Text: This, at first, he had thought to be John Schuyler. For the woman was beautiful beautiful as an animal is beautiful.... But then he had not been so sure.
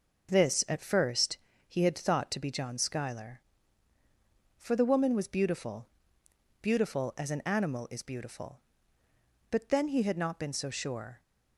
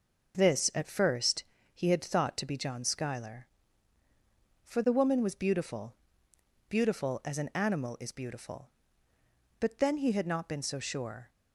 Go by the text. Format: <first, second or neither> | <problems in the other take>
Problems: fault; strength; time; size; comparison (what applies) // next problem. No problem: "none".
neither | pauses between "beautiful" and "beautiful"; noticeable; the same in both